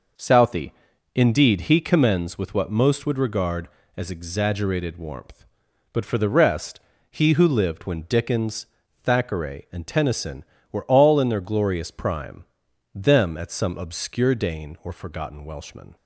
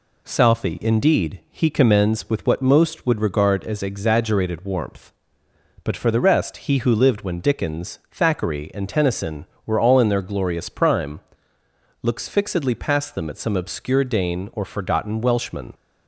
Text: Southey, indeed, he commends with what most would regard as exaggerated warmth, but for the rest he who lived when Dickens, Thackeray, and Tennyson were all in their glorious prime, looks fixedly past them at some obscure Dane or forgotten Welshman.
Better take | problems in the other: second | pauses between "rest" and "he"; slight; at 6.8 s; 0.30 s long // skips "looks fixedly past"; at 12.6 s

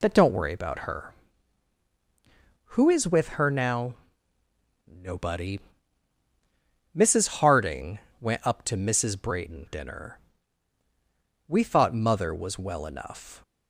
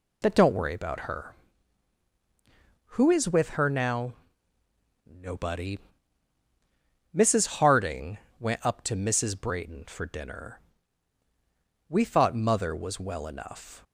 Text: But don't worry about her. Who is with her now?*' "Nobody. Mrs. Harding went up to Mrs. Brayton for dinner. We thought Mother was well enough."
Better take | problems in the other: second | pauses between "Harding" and "went"; slight; at 8.0 s; 0.20 s long; slight in the second // skips "for"; at 9.6 s

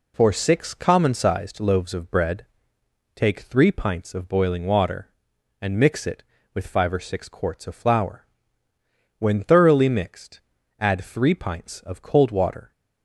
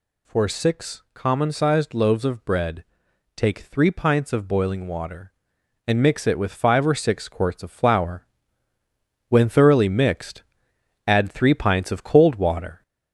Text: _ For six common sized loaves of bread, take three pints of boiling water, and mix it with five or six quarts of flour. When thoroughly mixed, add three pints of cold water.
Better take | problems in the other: first | gets louder; slight; throughout; 2.5 dB

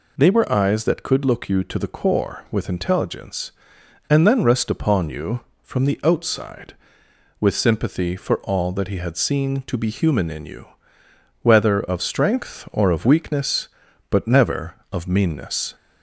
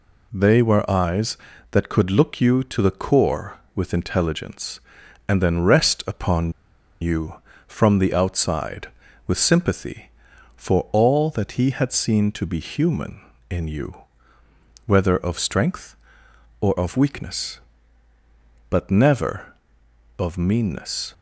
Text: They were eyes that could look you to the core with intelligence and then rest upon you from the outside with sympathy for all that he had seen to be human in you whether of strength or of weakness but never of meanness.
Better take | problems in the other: first | pauses between "upon" and "you"; noticeable; at 6.5 s; 0.49 s long // pauses between "you" and "whether"; noticeable; at 13.9 s; 0.92 s long; noticeable in the first

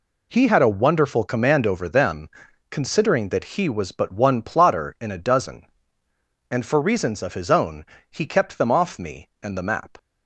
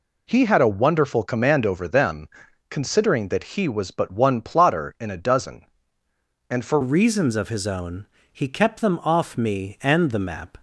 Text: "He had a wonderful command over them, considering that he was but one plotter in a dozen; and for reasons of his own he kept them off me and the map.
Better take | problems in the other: first | changes voice at "reasons"; from 6.8 s on; 3.7 s long // pauses between "own" and "he"; slight; at 8.0 s; 0.24 s long; slight in the first

